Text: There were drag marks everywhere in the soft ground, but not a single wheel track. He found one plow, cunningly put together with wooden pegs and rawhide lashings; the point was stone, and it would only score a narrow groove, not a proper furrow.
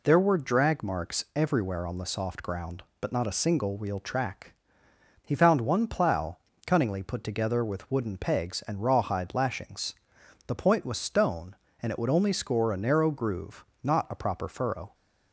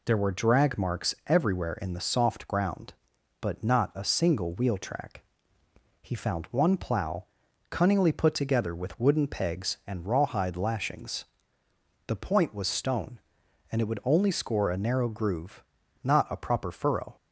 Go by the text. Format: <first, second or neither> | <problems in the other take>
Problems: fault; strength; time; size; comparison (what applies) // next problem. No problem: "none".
second | says "on" for "in"; at 1.8 s